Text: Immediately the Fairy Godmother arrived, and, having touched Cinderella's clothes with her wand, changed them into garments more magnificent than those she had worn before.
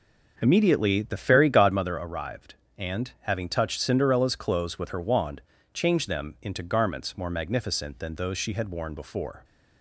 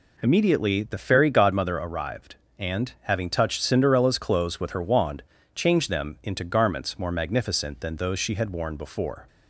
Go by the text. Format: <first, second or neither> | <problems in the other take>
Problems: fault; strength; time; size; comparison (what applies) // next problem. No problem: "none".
second | starts louder than the rest; noticeable; until 1.9 s; 5.5 dB